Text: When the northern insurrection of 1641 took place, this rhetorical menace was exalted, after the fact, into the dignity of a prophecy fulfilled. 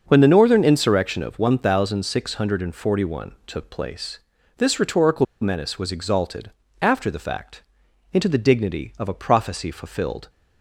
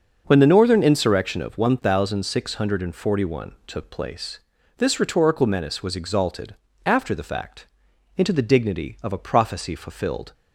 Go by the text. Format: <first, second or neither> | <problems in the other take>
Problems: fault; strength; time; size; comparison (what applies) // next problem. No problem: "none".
second | starts louder than the rest; until 1.0 s; 6.5 dB; also in the second // pauses between "rhetorical" and "menace"; slight; at 5.2 s; 0.17 s long